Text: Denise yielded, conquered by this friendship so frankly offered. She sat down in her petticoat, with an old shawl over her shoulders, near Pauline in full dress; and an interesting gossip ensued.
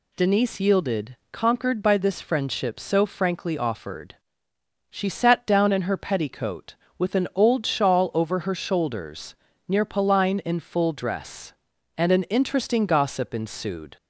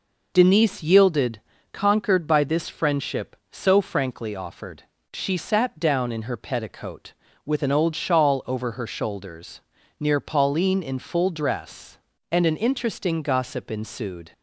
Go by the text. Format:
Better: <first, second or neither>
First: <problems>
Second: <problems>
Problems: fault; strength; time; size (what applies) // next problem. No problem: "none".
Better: neither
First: none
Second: none